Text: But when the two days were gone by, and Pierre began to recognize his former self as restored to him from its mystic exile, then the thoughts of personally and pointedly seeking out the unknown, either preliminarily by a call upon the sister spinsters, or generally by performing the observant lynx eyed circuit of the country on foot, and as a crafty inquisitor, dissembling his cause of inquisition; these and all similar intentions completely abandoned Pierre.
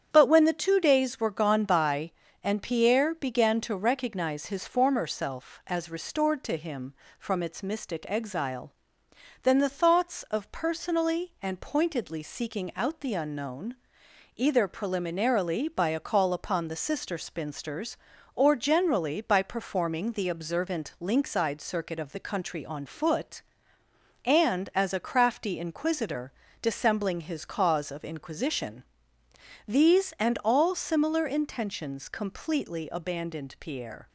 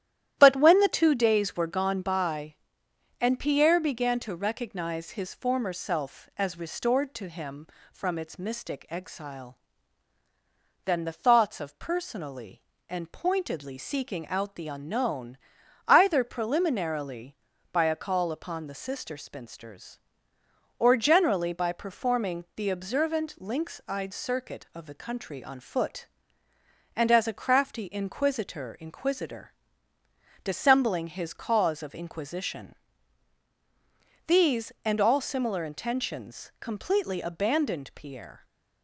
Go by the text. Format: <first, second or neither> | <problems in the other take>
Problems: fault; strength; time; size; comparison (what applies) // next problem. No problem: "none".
first | starts louder than the rest; strong; until 1.3 s; 12 dB; strong in the first // says "inquisitor" twice; at 28.7 s